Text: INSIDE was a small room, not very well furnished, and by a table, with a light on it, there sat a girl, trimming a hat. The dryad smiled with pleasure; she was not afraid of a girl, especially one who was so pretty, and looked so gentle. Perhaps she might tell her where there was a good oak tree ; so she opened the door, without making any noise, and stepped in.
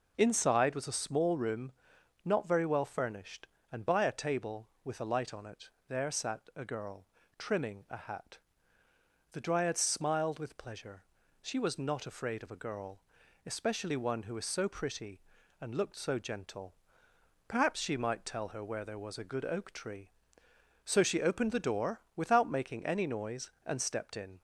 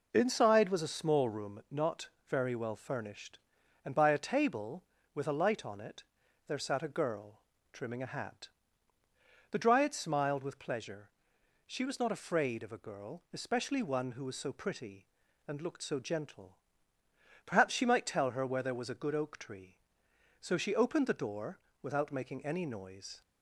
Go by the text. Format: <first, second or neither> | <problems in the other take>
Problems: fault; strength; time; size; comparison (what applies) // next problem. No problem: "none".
first | pauses between "not" and "very"; slight; at 2.0 s; 0.20 s long // stops before "and stepped in"; at 23.2 s